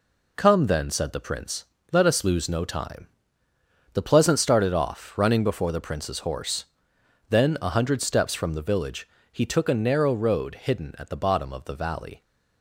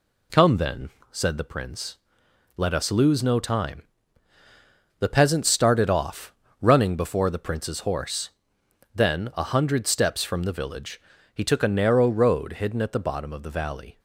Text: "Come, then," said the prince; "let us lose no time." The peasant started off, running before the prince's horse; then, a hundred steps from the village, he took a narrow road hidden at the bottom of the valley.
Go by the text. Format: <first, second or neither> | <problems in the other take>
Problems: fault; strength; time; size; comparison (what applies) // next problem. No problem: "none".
second | says "pleasant" for "peasant"; at 4.0 s